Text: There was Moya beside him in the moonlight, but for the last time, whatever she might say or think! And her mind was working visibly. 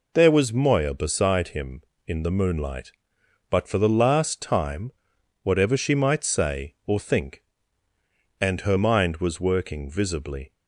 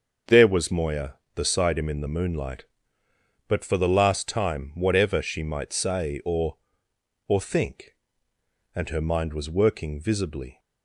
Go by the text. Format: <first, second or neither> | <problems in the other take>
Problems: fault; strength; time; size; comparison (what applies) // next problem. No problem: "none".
first | starts louder than the rest; until 1.4 s; 6.5 dB // says "or" twice; at 7.2 s